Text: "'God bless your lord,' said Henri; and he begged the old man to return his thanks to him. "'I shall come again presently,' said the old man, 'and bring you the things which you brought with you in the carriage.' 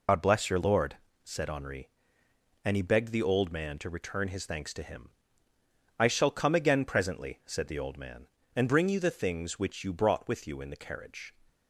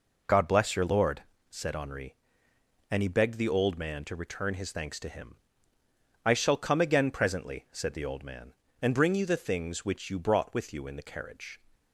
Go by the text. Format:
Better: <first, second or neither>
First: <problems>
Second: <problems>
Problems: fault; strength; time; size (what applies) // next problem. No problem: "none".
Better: second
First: loses the start of "God"; at 0.0 s; 80 ms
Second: none